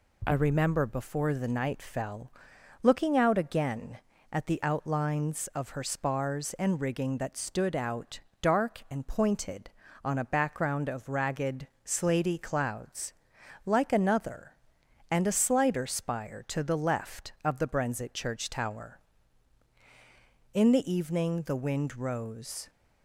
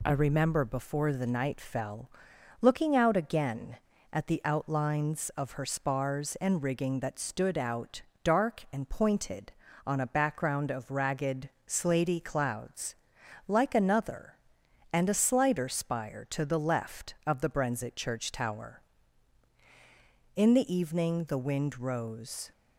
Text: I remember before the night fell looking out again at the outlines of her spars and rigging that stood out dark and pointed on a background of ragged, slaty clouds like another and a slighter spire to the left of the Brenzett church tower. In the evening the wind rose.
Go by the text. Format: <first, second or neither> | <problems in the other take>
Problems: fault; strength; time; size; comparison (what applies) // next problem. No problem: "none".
neither | pauses between "fell" and "looking"; noticeable; the same in both // pauses between "out" and "dark"; slight; the same in both // pauses between "clouds" and "like"; noticeable; the same in both